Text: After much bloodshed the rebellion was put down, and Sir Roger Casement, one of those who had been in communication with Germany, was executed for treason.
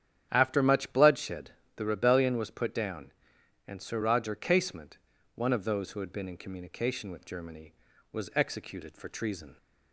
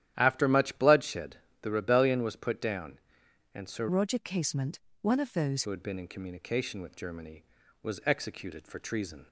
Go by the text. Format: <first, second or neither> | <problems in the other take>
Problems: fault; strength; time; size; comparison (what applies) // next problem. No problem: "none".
first | starts louder than the rest; strong; until 1.1 s; 11.5 dB; strong in the first // pauses between "bloodshed" and "the"; slight; at 1.3 s; 0.24 s long; slight in the first // changes voice from "Roger" to "those"; from 3.8 to 5.6 s; 1.8 s long